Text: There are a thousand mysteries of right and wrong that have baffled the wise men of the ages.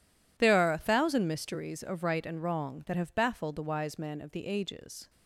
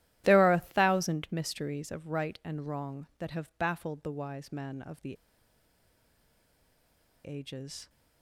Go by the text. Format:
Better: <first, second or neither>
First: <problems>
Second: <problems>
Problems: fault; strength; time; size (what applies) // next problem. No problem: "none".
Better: first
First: none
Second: starts louder than the rest; strong; until 1.2 s; 14 dB // pauses between "the" and "ages"; strong; at 5.1 s; 2.1 s long